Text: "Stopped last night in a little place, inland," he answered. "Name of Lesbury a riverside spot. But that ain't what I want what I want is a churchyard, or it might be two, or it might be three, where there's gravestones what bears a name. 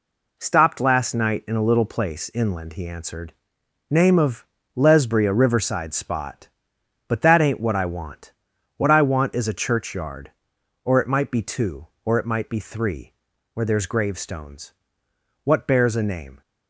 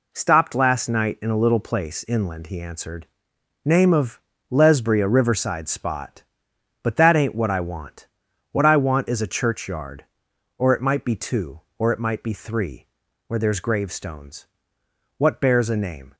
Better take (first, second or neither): neither